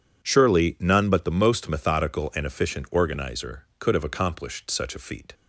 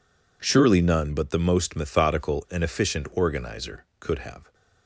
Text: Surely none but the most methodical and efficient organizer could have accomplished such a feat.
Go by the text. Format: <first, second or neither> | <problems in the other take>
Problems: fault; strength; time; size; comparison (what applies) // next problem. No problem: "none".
first | stops before "accomplished such a feat"; at 4.5 s